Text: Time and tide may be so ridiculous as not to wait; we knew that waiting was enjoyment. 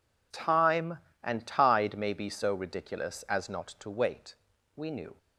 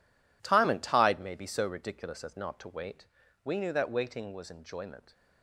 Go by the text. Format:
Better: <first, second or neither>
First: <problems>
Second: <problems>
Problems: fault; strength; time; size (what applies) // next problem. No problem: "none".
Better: second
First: stops before "that waiting was enjoyment"; at 5.1 s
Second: none